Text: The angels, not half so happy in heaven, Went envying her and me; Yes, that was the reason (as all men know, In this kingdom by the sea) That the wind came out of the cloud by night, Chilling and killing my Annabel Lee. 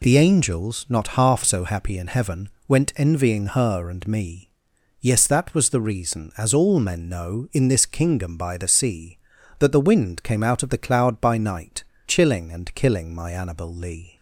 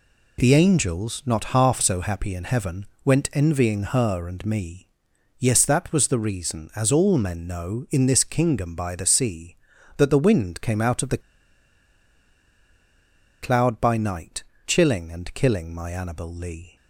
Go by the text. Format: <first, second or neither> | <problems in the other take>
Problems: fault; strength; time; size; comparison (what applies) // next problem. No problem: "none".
first | pauses between "the" and "cloud"; strong; at 11.2 s; 2.2 s long